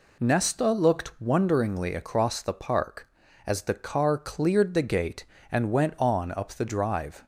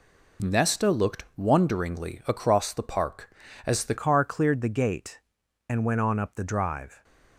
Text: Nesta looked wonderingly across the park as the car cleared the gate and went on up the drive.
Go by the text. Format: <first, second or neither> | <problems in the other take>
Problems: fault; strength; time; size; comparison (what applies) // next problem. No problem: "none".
first | changes voice at "car"; from 3.9 s on; 3.1 s long